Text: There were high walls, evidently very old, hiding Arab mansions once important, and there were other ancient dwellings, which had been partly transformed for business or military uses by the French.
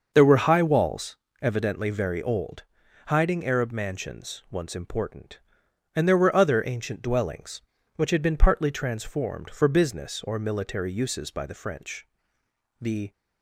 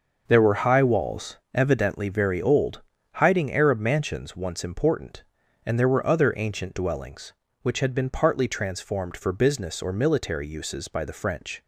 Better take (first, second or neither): second